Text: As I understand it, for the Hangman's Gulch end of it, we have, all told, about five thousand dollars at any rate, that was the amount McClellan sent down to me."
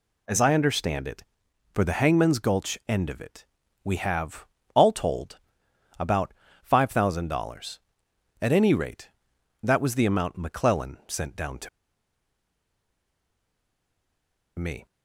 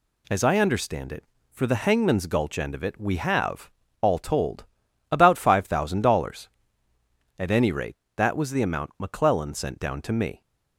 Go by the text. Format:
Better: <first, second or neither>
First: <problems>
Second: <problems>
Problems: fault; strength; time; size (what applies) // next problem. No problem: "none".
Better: second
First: pauses between "about" and "five"; slight; at 6.3 s; 0.30 s long // pauses between "to" and "me"; strong; at 11.6 s; 2.9 s long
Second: none